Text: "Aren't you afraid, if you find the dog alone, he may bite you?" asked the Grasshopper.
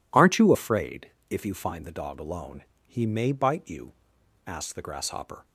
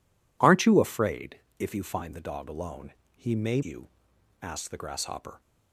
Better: first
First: none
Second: skips "bite"; at 3.6 s

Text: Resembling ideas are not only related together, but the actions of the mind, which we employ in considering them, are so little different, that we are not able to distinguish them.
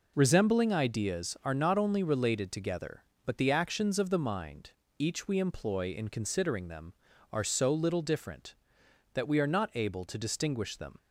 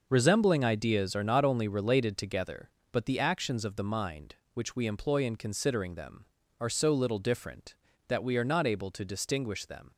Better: second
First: says "each" for "which"; at 4.9 s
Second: none

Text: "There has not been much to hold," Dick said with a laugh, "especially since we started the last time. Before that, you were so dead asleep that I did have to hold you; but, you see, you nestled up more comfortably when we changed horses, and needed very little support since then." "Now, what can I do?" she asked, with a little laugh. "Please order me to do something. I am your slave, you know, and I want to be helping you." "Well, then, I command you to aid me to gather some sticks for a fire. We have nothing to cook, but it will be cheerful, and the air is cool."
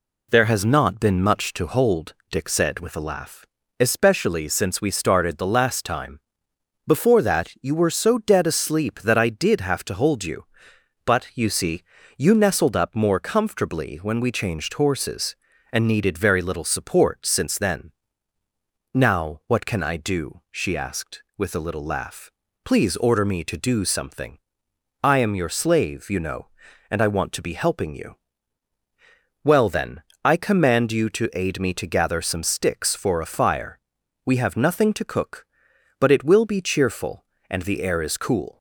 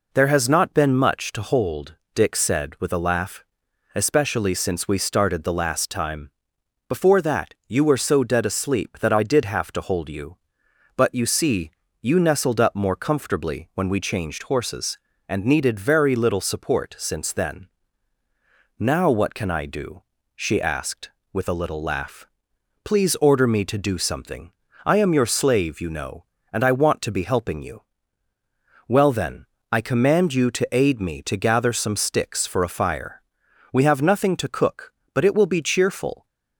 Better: first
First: none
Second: stops before "and the air is cool"; at 36.2 s

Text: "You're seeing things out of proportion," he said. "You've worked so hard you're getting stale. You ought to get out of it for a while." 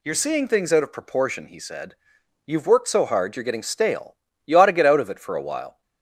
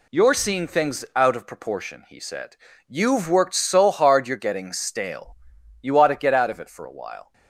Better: neither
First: none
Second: none

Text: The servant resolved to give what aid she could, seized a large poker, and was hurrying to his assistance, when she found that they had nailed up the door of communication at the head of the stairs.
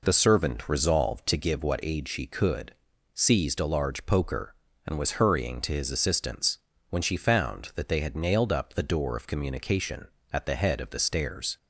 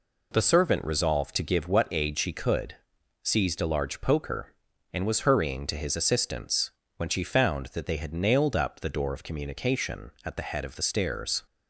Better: neither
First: none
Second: none

